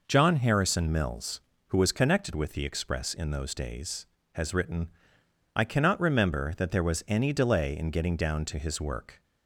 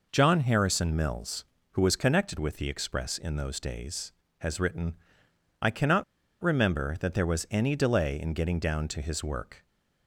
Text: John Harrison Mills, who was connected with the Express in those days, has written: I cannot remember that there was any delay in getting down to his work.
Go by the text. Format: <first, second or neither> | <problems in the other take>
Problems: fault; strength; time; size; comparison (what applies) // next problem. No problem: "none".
first | pauses between "cannot" and "remember"; at 6.0 s; 0.39 s long